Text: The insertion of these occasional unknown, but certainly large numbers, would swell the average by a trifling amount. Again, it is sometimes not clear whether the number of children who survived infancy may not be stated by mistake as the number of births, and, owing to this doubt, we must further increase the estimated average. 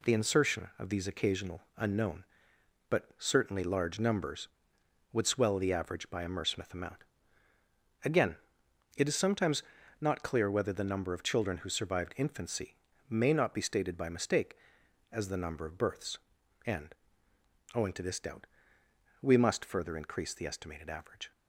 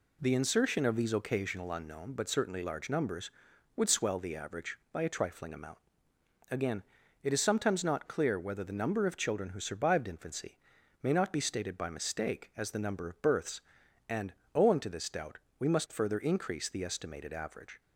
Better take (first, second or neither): second